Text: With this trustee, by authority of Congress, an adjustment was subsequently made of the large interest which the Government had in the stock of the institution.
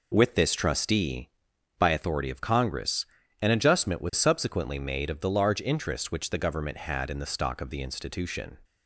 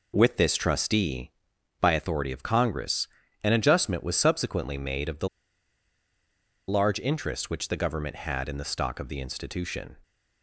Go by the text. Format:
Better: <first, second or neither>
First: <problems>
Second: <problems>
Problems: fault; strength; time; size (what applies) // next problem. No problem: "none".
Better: first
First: none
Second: pauses between "the" and "large"; strong; at 5.2 s; 1.4 s long